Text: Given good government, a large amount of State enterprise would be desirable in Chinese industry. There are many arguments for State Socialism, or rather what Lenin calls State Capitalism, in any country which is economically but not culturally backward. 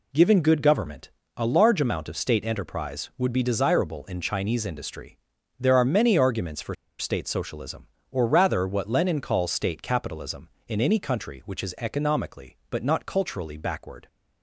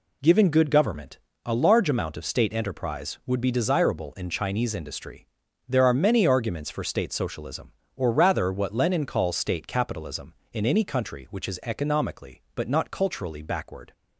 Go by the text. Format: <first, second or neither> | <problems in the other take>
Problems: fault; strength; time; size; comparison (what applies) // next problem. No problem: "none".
second | pauses between "for" and "State"; slight; at 6.7 s; 0.25 s long